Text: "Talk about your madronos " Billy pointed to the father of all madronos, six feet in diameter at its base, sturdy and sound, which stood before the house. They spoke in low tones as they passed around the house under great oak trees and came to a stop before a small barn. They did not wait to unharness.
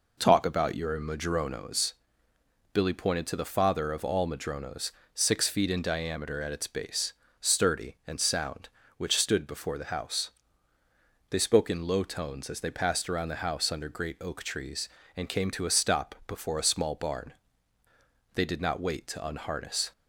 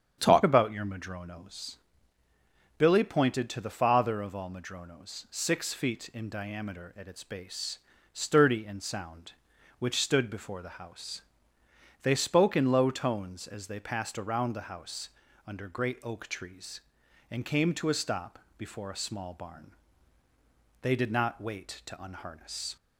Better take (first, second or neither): first